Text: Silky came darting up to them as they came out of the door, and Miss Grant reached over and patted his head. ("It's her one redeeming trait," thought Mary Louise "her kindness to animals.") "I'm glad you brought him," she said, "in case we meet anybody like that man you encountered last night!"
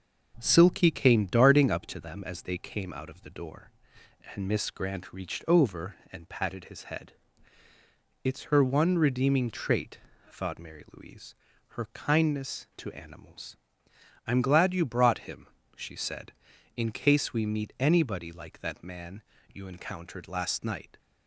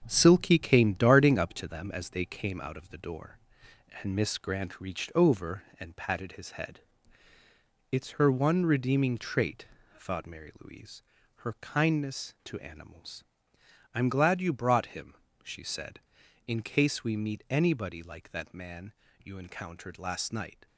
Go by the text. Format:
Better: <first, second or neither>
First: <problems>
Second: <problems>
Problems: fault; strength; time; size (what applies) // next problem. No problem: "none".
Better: first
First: starts louder than the rest; noticeable; until 1.4 s; 6 dB // pauses between "Louise" and "her"; slight; at 11.3 s; 0.34 s long // pauses between "man" and "you"; slight; at 19.2 s; 0.32 s long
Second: gets quieter; throughout; 6.5 dB // starts louder than the rest; strong; until 1.0 s; 7 dB // pauses between "Louise" and "her"; slight; at 11.0 s; 0.34 s long // pauses between "man" and "you"; slight; at 18.9 s; 0.32 s long